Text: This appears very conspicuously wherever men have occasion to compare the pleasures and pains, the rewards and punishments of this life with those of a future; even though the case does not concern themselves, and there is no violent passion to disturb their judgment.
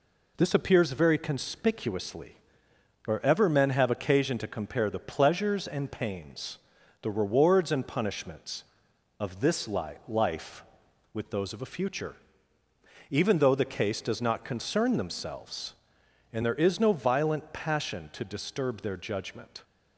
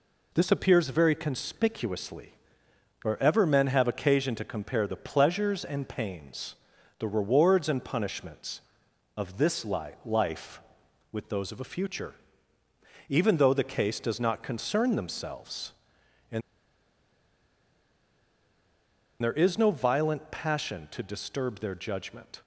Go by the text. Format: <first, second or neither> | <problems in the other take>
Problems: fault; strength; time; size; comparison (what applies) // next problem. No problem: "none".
first | pauses between "conspicuously" and "wherever"; noticeable; at 2.3 s; 0.68 s long; noticeable in the first // pauses between "and" and "there"; strong; at 16.4 s; 2.8 s long